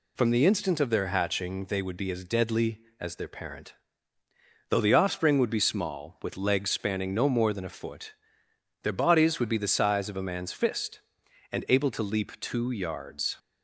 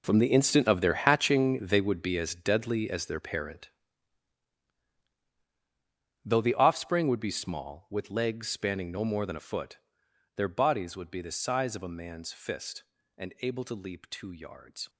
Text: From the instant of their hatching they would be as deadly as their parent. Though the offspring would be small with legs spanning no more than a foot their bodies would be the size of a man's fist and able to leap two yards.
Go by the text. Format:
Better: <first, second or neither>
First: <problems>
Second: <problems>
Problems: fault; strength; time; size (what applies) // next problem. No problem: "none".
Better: first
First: pauses between "foot" and "their"; noticeable; at 8.1 s; 0.70 s long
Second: gets quieter; strong; throughout; 14 dB // pauses between "foot" and "their"; noticeable; at 9.7 s; 0.60 s long